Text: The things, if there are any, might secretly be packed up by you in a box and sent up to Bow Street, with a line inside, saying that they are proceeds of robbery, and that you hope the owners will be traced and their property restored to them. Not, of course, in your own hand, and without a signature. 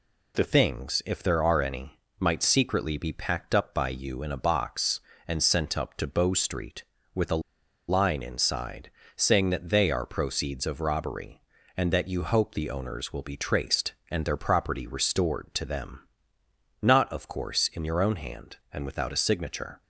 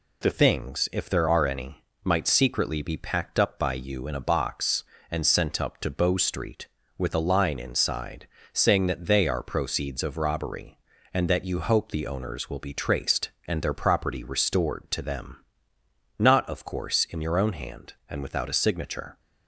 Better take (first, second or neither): second